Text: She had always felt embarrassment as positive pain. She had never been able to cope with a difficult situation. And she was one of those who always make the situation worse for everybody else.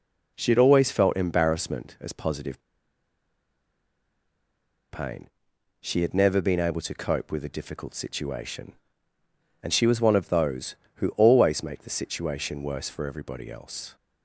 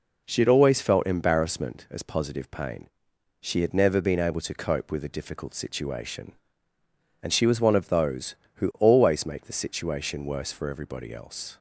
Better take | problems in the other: second | pauses between "positive" and "pain"; strong; at 2.5 s; 2.3 s long

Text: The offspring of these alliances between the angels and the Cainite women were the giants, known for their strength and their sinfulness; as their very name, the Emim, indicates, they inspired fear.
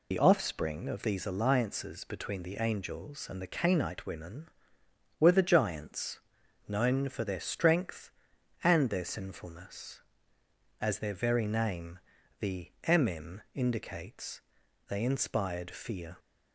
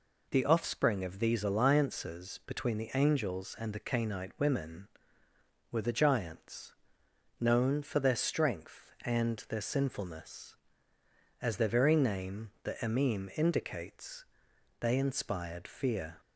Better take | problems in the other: second | loses the start of "The"; at 0.1 s; 60 ms

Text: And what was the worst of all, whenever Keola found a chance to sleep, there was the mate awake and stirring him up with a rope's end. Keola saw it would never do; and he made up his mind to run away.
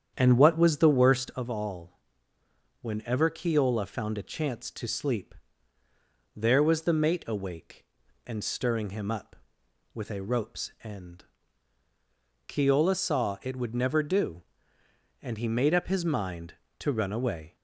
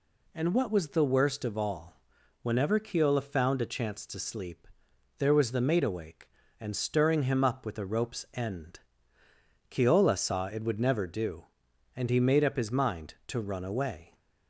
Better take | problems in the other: second | starts louder than the rest; strong; until 1.4 s; 8.5 dB

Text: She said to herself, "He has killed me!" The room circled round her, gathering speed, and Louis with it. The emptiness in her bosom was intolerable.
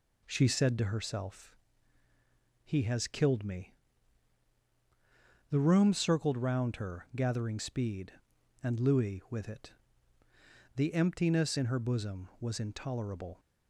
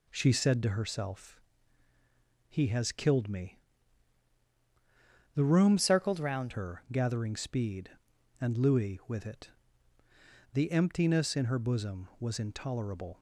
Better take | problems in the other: first | changes voice from "circled" to "round"; from 5.7 to 6.5 s; 0.8 s long

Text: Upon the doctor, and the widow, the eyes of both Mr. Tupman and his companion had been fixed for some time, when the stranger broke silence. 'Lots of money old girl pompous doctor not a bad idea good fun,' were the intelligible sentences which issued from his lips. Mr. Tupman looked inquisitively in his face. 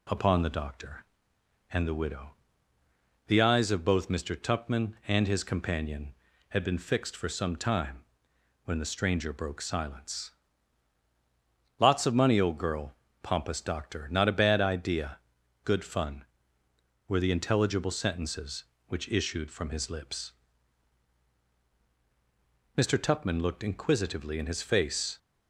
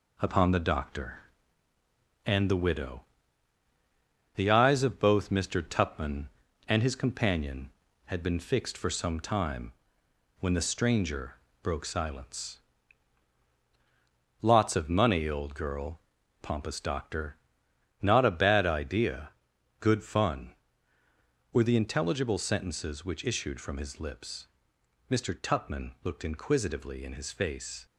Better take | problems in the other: first | gets quieter; noticeable; throughout; 4 dB // pauses between "stranger" and "broke"; slight; at 11.3 s; 0.26 s long // pauses between "girl" and "pompous"; at 15.9 s; 0.42 s long; slight in the first // pauses between "doctor" and "not"; noticeable; at 17.3 s; 0.66 s long // pauses between "idea" and "good"; noticeable; at 19.2 s; 0.50 s long; noticeable in the first

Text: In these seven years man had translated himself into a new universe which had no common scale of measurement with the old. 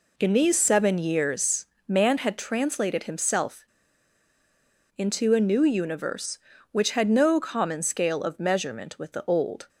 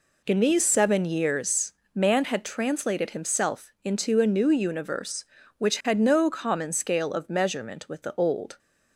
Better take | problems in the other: second | pauses between "years" and "man"; slight; at 1.6 s; 0.24 s long; slight in the second // pauses between "himself" and "into"; strong; at 3.6 s; 1.3 s long

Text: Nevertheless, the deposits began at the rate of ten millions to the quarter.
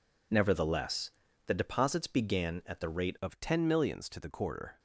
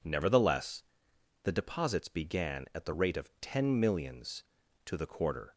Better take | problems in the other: second | changes voice at "of"; from 3.2 s on; 1.5 s long

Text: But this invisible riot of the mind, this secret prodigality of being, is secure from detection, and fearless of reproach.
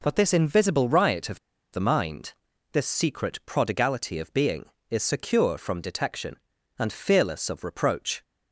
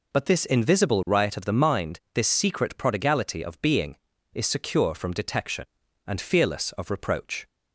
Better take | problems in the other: second | pauses between "of" and "the"; slight; at 1.3 s; 0.34 s long

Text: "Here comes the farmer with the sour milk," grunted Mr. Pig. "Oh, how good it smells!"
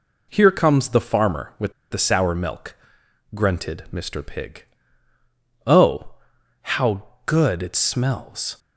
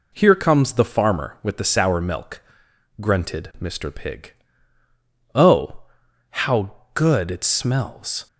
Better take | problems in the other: second | pauses between "with" and "the"; slight; at 1.7 s; 0.18 s long // pauses between "how" and "good"; slight; at 7.0 s; 0.22 s long; slight in the second

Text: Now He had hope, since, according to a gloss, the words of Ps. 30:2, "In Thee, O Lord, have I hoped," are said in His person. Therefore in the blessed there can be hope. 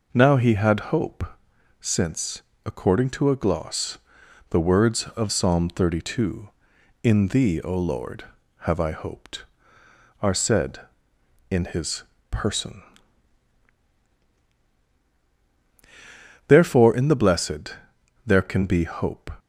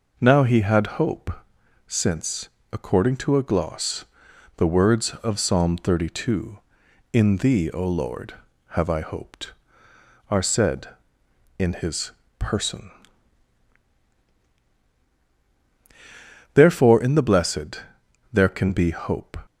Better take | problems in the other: neither | pauses between "His" and "person"; slight; the same in both // pauses between "blessed" and "there"; noticeable; the same in both

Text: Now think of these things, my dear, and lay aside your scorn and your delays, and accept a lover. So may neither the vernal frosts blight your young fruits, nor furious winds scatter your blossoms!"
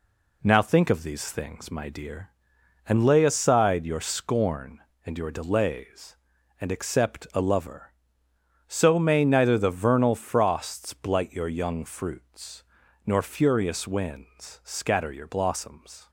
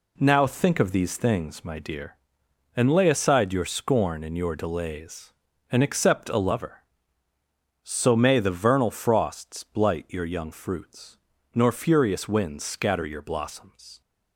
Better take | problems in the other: first | skips "neither"; at 8.3 s

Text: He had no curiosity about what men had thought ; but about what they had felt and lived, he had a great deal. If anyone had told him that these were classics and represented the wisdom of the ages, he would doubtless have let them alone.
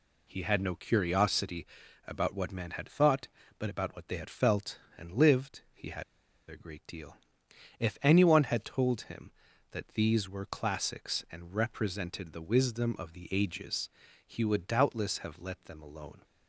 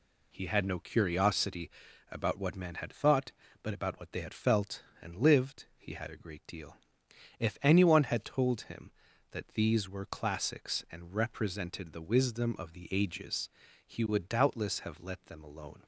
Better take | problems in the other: second | pauses between "curiosity" and "about"; at 1.6 s; 0.40 s long; also in the second // pauses between "had" and "a"; noticeable; at 6.0 s; 0.46 s long

